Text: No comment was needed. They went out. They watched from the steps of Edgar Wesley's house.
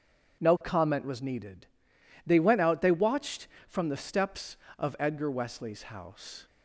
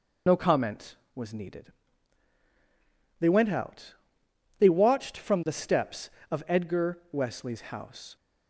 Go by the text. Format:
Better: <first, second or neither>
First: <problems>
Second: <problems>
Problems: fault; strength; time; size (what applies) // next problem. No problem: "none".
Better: first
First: none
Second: loses the start of "No"; at 0.2 s; 65 ms